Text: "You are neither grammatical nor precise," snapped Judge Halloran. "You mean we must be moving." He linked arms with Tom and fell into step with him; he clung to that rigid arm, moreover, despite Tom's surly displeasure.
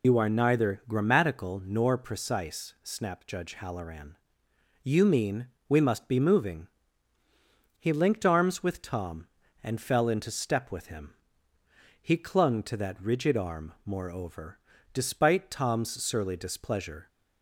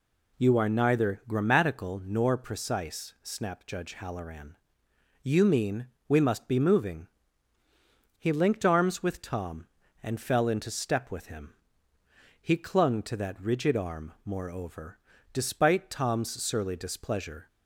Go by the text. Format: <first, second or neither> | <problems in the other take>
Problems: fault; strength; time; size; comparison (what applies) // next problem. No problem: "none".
second | loses the start of "You"; at 0.0 s; 90 ms // pauses between "mean" and "we"; slight; at 5.4 s; 0.18 s long; slight in the second